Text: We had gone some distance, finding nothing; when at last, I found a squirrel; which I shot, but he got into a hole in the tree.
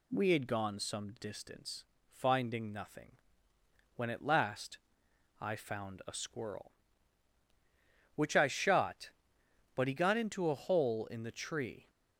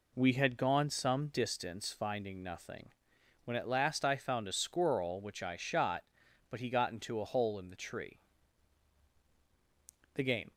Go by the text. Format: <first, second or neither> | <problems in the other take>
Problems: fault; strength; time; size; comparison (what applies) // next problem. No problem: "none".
first | goes on to say "The game"; slight; from 10.1 s on; 0.40 s long